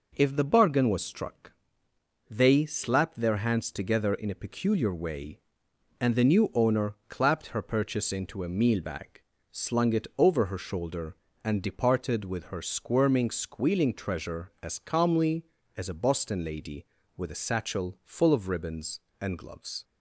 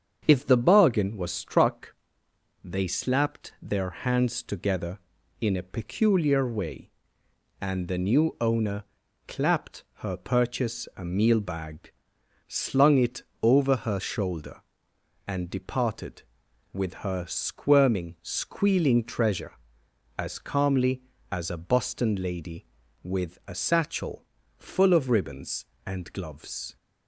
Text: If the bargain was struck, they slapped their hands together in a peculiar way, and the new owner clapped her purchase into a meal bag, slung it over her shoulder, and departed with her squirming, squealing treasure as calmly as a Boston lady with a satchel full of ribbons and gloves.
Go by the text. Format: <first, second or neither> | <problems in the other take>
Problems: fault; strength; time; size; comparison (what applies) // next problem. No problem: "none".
first | starts louder than the rest; strong; until 1.2 s; 7.5 dB // pauses between "owner" and "clapped"; at 8.8 s; 0.44 s long // skips "into"; at 10.9 s // pauses between "it" and "over"; slight; at 13.2 s; 0.18 s long // pauses between "satchel" and "full"; slight; at 24.2 s; 0.34 s long